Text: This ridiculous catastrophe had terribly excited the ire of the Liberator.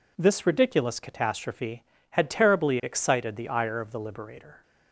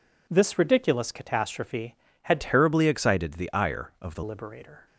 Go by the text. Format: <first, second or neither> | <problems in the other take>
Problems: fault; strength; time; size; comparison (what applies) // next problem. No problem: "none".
first | changes voice from "terribly" to "the"; from 2.3 to 4.2 s; 1.9 s long